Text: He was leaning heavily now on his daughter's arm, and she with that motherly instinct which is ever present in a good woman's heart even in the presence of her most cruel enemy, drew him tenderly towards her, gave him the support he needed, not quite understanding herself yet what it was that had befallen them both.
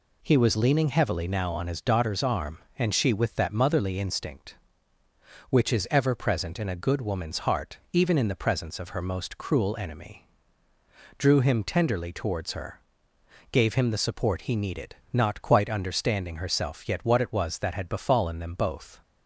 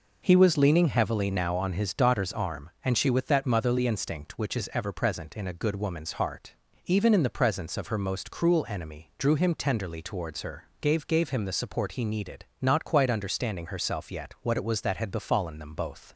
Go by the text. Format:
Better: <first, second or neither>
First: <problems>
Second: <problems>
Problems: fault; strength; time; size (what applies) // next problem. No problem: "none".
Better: first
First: pauses between "heart" and "even"; slight; at 7.7 s; 0.16 s long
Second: pauses between "heart" and "even"; slight; at 6.5 s; 0.32 s long // says "gave" twice; at 11.0 s